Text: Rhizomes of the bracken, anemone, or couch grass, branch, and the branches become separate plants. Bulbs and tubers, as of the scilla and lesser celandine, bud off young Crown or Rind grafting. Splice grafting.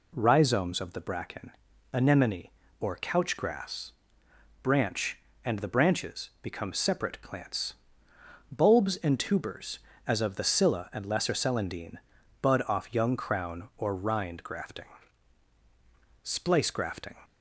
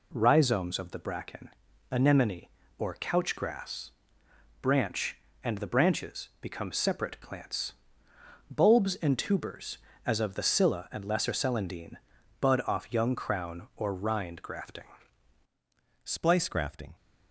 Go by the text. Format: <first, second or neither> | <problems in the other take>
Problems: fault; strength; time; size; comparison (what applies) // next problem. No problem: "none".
first | changes voice at "Splice"; from 16.0 s on; 0.9 s long